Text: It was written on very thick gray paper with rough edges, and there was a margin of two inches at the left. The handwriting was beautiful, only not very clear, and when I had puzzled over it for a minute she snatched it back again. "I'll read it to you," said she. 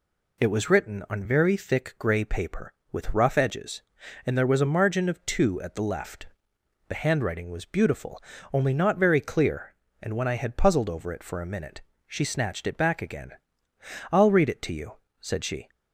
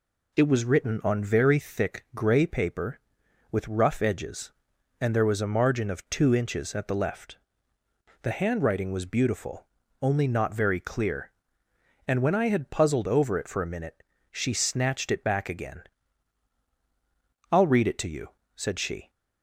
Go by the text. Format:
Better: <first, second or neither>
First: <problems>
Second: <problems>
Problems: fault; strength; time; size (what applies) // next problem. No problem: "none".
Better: second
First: skips "inches"; at 5.6 s // pauses between "minute" and "she"; slight; at 11.8 s; 0.24 s long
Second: pauses between "minute" and "she"; slight; at 14.0 s; 0.32 s long